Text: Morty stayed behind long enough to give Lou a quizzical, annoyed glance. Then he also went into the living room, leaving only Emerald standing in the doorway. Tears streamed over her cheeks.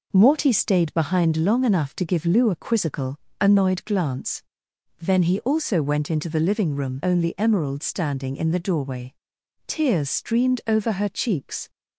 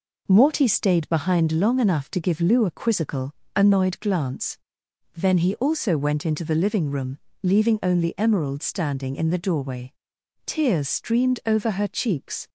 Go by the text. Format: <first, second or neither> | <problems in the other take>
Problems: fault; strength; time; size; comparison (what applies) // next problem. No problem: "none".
second | skips "leaving"; at 7.0 s